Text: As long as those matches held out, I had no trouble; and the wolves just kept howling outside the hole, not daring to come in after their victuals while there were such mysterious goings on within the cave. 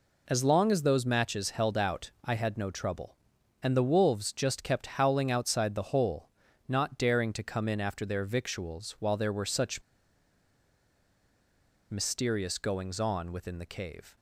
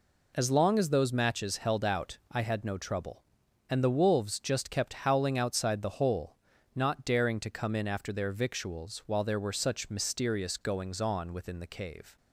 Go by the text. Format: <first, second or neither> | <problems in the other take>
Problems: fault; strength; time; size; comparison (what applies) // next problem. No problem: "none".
second | pauses between "such" and "mysterious"; strong; at 9.8 s; 2.0 s long